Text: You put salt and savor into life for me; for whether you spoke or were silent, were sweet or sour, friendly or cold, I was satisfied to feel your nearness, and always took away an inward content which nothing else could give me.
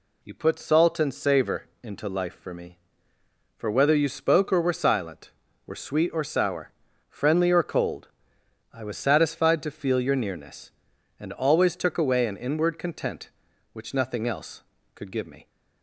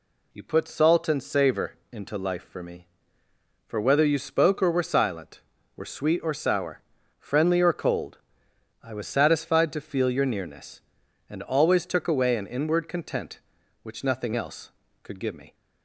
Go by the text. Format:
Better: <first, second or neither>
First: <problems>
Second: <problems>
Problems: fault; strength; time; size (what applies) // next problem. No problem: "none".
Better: neither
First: pauses between "savor" and "into"; slight; at 1.6 s; 0.16 s long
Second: pauses between "savor" and "into"; slight; at 1.7 s; 0.16 s long